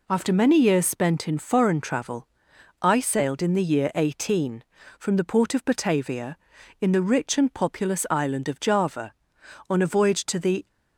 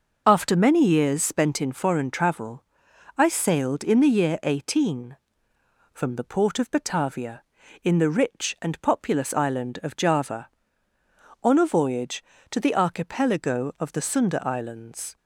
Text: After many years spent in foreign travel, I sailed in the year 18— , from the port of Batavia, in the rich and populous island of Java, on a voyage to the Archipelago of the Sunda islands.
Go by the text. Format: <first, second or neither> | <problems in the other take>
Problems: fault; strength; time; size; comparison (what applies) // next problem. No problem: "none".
second | stops before "Archipelago of the Sunda islands"; at 10.6 s